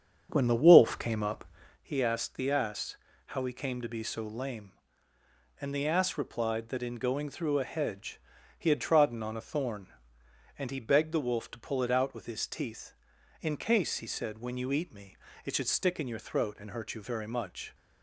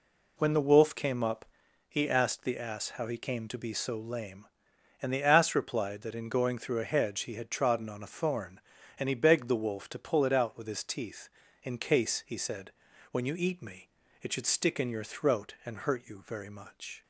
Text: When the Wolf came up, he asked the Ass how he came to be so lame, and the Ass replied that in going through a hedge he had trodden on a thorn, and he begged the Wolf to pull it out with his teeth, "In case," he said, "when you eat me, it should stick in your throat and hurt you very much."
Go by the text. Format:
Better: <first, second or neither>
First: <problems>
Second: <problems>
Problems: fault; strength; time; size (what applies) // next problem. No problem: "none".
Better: second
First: starts louder than the rest; until 1.8 s; 7 dB // pauses between "Ass" and "how"; slight; at 2.9 s; 0.30 s long // pauses between "hedge" and "he"; slight; at 8.2 s; 0.36 s long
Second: none